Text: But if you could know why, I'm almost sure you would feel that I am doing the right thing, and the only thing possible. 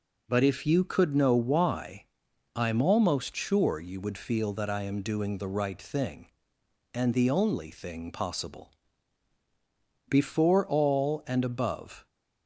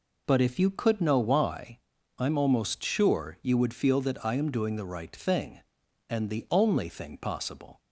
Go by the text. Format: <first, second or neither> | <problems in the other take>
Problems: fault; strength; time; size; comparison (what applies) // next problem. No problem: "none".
second | goes on to say "Before all and above"; strong; from 10.3 s on; 1.7 s long